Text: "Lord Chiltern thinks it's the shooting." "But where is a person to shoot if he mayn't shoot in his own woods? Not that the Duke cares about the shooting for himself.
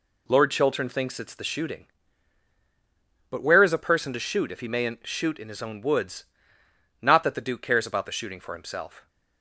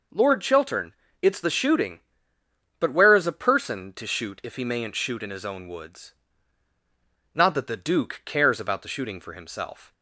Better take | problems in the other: first | skips "thinks"; at 1.0 s

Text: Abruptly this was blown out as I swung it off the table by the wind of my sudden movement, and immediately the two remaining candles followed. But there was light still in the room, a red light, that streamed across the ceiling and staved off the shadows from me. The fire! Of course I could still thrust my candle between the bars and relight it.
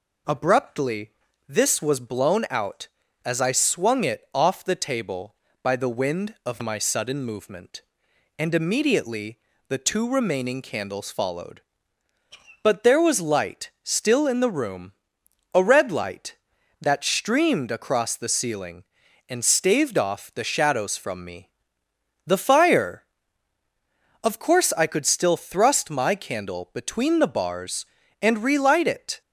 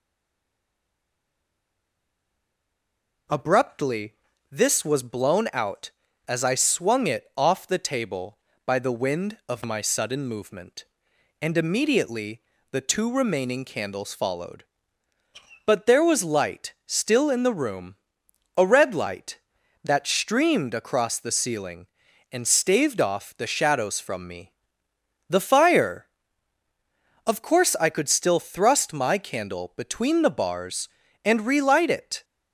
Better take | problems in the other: first | stays silent before the first word; strong; until 3.2 s; 3.2 s long // pauses between "Abruptly" and "this"; slight; at 4.1 s; 0.36 s long; slight in the first // pauses between "immediately" and "the"; slight; at 12.3 s; 0.32 s long; slight in the first

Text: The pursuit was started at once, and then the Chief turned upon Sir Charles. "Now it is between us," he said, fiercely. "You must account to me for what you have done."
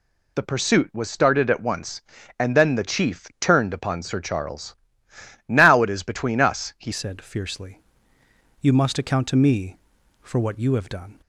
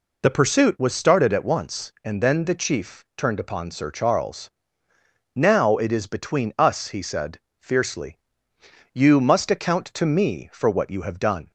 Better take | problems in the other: second | changes voice at "said"; from 6.9 s on; 4.3 s long

